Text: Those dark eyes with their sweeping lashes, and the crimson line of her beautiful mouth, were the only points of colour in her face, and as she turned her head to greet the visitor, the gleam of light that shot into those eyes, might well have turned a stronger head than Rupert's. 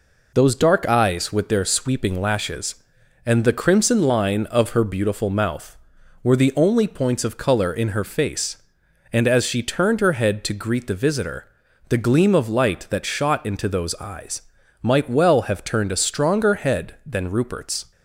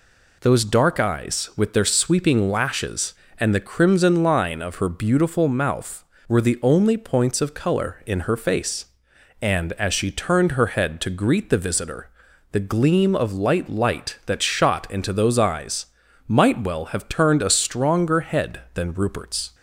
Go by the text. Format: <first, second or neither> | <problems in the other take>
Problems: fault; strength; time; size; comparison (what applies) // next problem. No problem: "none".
first | says "light" twice; at 13.6 s